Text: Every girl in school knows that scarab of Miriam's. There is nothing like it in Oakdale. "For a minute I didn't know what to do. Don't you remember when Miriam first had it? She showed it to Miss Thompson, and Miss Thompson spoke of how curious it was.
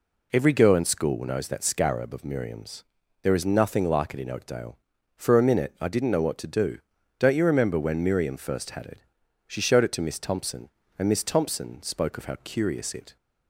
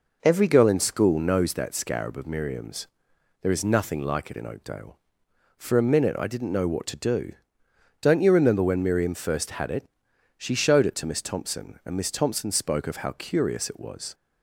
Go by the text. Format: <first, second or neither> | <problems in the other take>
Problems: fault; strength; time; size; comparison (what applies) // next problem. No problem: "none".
second | stops before "was"; at 13.1 s